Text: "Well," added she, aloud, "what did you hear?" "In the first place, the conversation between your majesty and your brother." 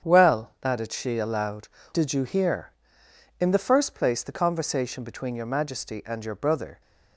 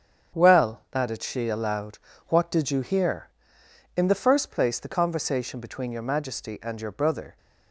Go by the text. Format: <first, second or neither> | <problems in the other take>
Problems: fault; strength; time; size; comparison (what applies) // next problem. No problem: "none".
second | starts louder than the rest; strong; until 1.1 s; 8 dB; strong in the second // skips "what"; at 1.8 s